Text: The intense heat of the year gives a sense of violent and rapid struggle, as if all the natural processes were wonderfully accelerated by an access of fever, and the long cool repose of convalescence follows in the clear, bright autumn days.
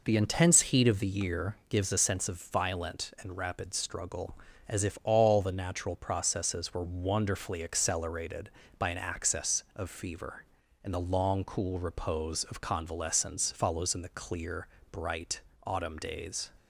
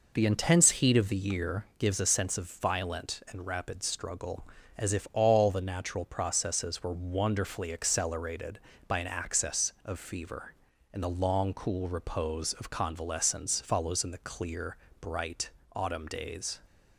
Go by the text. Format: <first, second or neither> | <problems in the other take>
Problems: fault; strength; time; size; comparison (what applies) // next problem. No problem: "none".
neither | pauses between "bright" and "autumn"; slight; the same in both